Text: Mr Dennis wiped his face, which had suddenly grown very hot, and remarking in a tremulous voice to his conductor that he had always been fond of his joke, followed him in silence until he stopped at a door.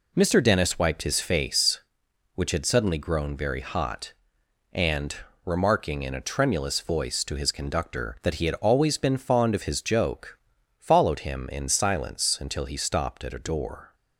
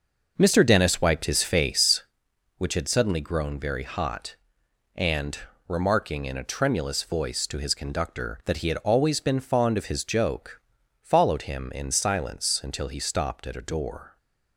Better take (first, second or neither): first